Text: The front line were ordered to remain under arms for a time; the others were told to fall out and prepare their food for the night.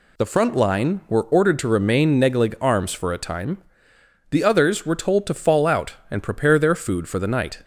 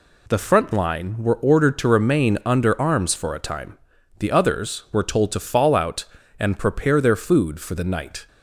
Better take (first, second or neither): second